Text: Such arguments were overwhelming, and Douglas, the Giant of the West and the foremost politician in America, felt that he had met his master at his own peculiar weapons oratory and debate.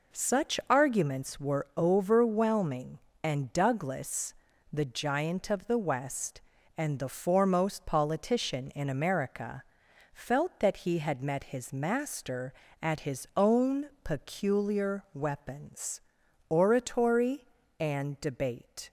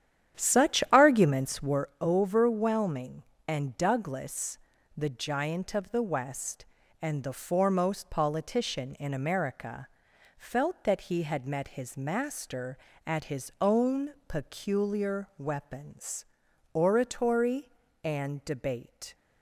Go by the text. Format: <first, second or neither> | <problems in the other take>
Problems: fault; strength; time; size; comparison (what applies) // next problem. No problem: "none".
first | starts louder than the rest; strong; until 1.8 s; 10 dB // pauses between "own" and "peculiar"; slight; at 14.1 s; 0.16 s long; slight in the first // pauses between "weapons" and "oratory"; noticeable; at 16.2 s; 0.48 s long; noticeable in the first